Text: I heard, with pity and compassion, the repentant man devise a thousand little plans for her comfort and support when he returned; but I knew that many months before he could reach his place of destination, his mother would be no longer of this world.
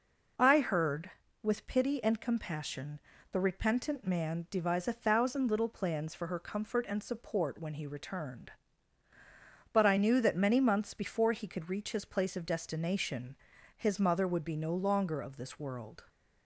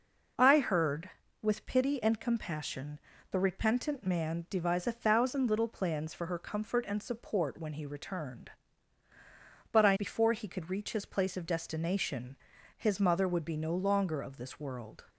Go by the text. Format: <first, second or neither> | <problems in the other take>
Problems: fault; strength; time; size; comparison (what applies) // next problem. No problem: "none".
first | skips "knew that many months"; at 9.9 s